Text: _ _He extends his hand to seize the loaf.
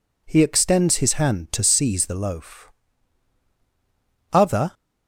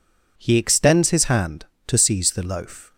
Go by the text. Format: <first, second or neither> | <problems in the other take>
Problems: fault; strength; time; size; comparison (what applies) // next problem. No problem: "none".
second | goes on to say "Other"; slight; from 4.3 s on; 0.42 s long